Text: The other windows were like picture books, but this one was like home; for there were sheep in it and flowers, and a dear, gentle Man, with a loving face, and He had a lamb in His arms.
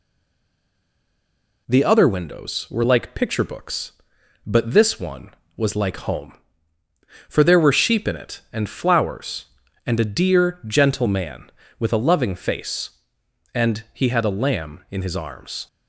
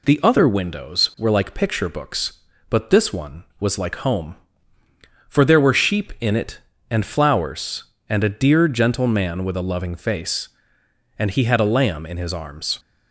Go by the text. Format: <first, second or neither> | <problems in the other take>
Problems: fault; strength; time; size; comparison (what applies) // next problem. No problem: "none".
second | stays silent before the first word; noticeable; until 1.6 s; 1.6 s long